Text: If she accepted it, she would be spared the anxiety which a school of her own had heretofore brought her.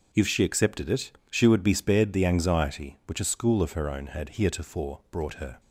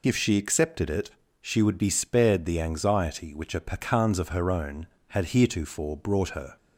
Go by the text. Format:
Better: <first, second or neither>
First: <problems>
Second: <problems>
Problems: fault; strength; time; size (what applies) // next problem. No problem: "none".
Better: first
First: none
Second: says "pecans" for "school"; at 3.6 s